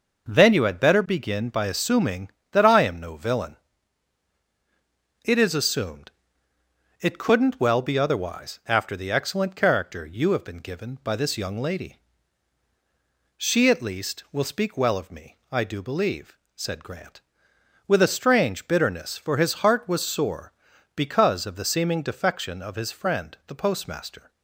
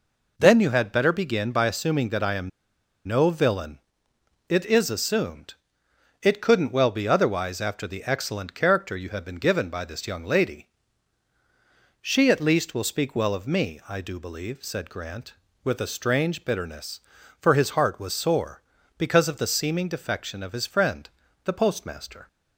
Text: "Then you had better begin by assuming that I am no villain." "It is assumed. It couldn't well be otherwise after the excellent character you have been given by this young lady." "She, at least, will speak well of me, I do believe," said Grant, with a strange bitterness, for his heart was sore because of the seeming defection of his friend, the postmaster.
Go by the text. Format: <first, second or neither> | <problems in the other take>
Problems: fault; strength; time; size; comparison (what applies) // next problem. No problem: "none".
first | pauses between "am" and "no"; noticeable; at 2.5 s; 0.57 s long